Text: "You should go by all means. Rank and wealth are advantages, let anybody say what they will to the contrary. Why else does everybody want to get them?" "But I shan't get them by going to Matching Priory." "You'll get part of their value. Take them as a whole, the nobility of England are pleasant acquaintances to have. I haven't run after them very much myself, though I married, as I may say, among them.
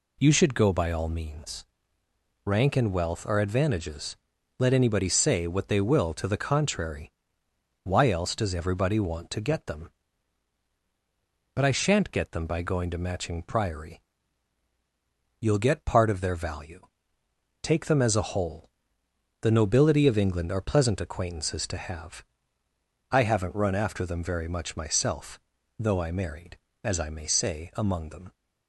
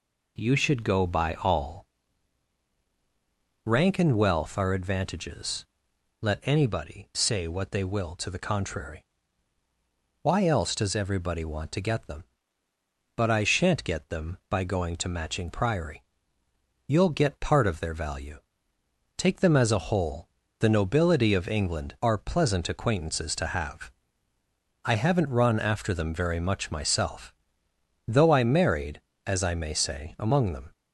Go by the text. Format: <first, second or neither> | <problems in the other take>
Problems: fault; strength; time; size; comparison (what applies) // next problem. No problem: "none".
first | skips "means"; at 2.7 s